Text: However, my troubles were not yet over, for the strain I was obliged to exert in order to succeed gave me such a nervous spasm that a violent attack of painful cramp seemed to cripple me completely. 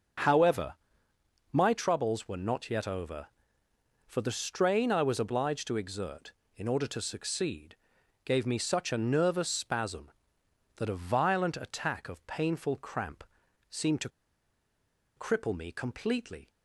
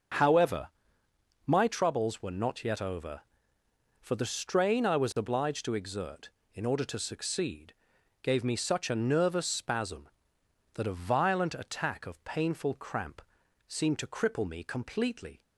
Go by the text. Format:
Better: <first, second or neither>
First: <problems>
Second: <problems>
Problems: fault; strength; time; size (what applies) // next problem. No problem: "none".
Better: second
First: starts louder than the rest; until 2.0 s; 7 dB // pauses between "succeed" and "gave"; noticeable; at 7.7 s; 0.48 s long // pauses between "cramp" and "seemed"; noticeable; at 13.2 s; 0.48 s long // pauses between "to" and "cripple"; at 14.0 s; 1.0 s long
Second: starts louder than the rest; until 1.9 s; 6.5 dB // pauses between "succeed" and "gave"; noticeable; at 7.7 s; 0.48 s long // pauses between "cramp" and "seemed"; noticeable; at 13.2 s; 0.48 s long